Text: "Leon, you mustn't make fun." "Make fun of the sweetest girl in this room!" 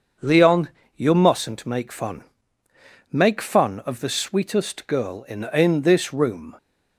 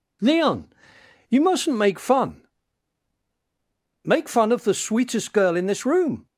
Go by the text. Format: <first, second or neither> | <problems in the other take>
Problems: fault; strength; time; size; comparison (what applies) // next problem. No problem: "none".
second | starts louder than the rest; until 1.4 s; 6.5 dB // says "in" twice; at 5.5 s